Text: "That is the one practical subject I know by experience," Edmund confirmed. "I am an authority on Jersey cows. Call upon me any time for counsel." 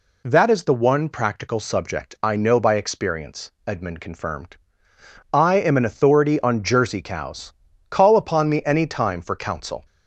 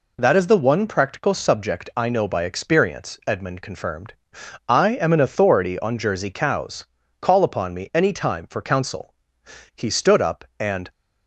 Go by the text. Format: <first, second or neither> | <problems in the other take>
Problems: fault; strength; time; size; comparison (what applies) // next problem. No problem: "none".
first | goes on to say "He stood up and"; noticeable; from 9.7 s on; 1.1 s long